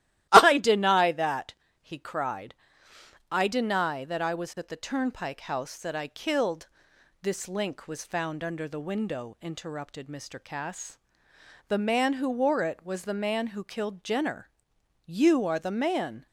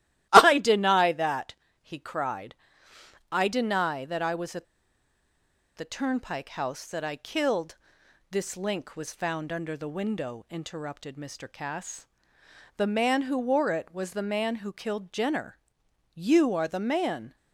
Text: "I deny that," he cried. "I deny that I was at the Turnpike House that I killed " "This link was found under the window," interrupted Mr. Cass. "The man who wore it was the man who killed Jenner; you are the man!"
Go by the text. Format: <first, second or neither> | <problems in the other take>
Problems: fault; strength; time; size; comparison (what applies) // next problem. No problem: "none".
first | starts louder than the rest; strong; until 1.3 s; 15 dB; strong in the first // pauses between "at" and "the"; at 4.6 s; 1.1 s long